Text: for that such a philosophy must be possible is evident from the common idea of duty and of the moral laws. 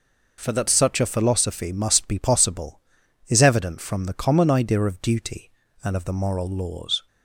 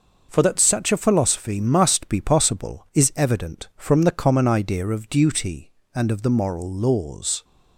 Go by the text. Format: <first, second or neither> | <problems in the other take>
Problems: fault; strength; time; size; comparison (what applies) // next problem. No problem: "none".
neither | none